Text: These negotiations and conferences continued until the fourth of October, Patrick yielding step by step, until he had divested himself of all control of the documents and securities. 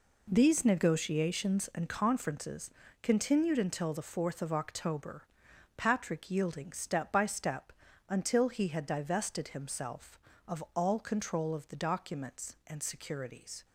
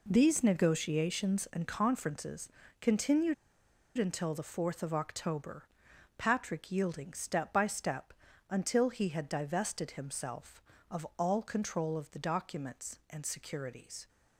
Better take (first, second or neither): first